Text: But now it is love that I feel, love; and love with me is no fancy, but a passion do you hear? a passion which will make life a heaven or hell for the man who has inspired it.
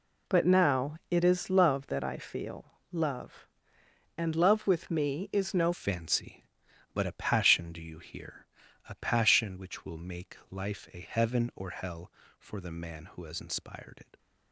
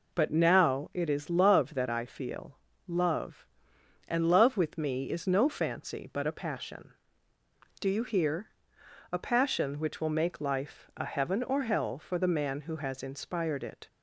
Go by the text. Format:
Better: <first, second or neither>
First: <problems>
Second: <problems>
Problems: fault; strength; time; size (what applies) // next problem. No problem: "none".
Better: second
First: pauses between "now" and "it"; slight; at 0.9 s; 0.16 s long // changes voice at "fancy"; from 5.7 s on; 8.4 s long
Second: none